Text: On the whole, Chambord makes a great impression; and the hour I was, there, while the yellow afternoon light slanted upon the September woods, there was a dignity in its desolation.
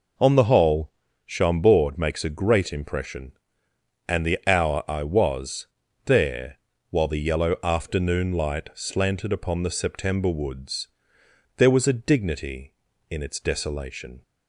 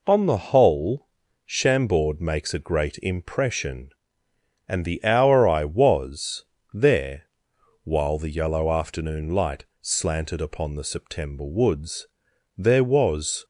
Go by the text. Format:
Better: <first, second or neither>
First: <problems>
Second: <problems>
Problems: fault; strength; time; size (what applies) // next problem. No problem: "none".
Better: first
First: none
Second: pauses between "light" and "slanted"; slight; at 9.6 s; 0.16 s long // stops before "a dignity in its desolation"; at 13.4 s